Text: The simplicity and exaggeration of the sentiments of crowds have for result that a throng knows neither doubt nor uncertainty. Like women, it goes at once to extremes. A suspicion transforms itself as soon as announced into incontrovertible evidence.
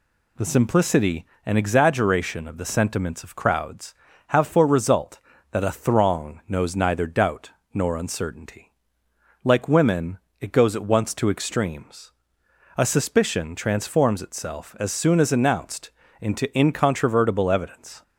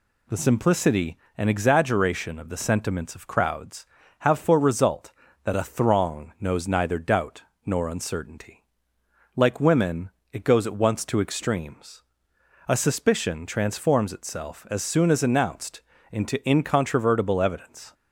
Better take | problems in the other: neither | pauses between "doubt" and "nor"; slight; the same in both // pauses between "announced" and "into"; slight; the same in both

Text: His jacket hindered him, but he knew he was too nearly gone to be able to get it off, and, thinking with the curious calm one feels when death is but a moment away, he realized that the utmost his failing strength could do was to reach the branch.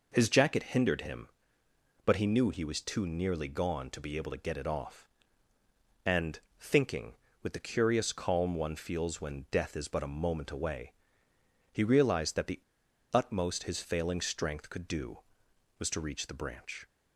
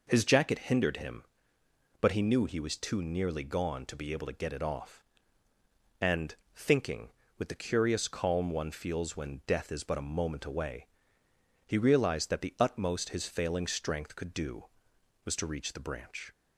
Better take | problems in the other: second | pauses between "the" and "utmost"; noticeable; at 12.6 s; 0.52 s long

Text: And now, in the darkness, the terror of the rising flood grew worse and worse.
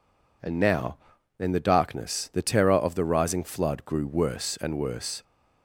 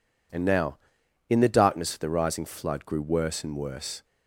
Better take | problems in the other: first | skips "the terror"; at 1.9 s

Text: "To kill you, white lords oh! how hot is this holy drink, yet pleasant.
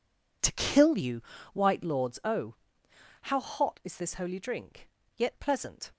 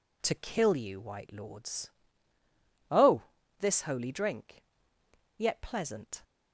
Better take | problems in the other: first | pauses between "lords" and "oh"; at 1.9 s; 1.0 s long // skips "how hot is"; at 3.4 s

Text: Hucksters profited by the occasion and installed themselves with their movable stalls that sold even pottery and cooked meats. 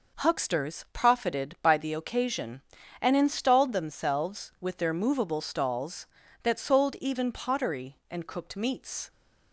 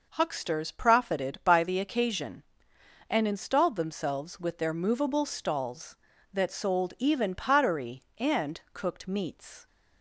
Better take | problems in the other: neither | none

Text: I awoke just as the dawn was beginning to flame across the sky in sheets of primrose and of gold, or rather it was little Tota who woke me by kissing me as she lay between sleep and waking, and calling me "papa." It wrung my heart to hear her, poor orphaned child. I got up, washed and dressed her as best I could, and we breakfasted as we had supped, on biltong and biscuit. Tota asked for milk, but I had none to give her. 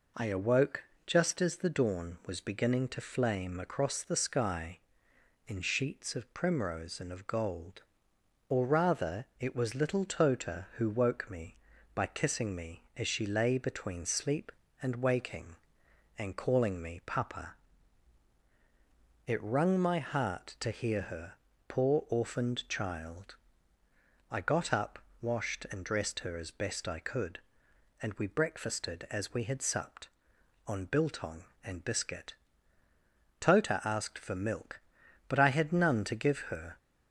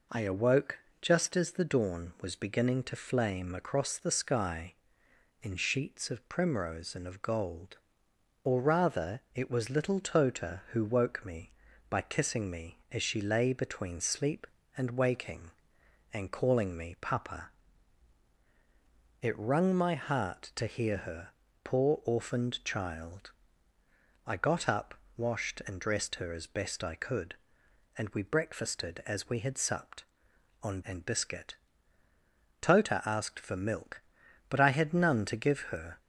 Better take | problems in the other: first | pauses between "awoke" and "just"; slight; at 0.7 s; 0.22 s long; slight in the first // skips "biltong"; at 30.8 s

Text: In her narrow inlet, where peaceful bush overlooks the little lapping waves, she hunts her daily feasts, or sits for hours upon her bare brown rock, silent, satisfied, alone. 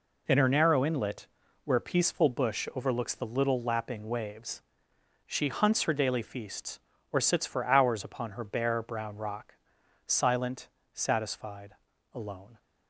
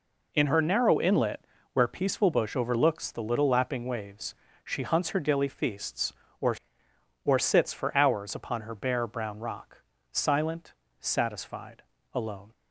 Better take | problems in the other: first | says "or" twice; at 7.2 s

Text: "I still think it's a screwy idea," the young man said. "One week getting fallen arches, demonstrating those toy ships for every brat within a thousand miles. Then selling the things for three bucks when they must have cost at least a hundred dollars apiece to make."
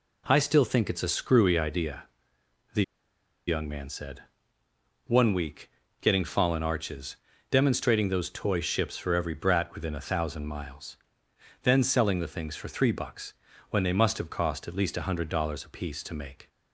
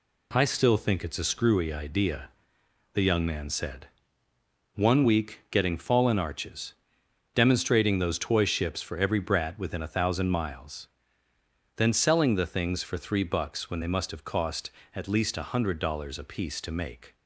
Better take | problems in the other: second | pauses between "the" and "young"; noticeable; at 2.8 s; 0.63 s long // pauses between "week" and "getting"; slight; at 5.6 s; 0.32 s long // pauses between "bucks" and "when"; at 13.3 s; 0.38 s long

